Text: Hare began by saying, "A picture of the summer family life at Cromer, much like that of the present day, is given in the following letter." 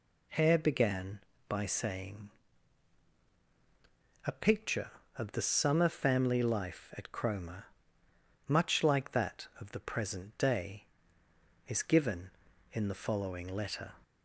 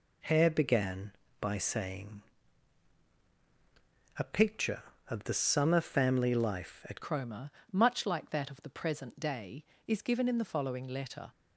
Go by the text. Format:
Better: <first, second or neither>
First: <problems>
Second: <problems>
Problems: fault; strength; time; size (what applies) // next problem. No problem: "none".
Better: first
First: none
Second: changes voice at "Cromer"; from 7.0 s on; 4.3 s long